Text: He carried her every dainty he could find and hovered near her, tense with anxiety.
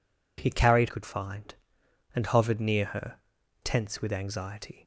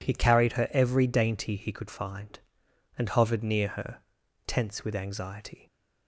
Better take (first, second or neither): second